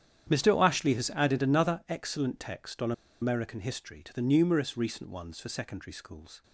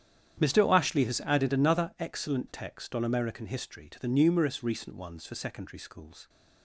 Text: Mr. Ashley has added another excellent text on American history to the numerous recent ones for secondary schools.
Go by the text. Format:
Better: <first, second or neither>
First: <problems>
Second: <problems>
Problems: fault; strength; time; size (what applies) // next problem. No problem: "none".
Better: second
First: starts louder than the rest; strong; until 1.4 s; 9 dB // pauses between "on" and "American"; slight; at 2.9 s; 0.29 s long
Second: starts louder than the rest; strong; until 1.5 s; 9 dB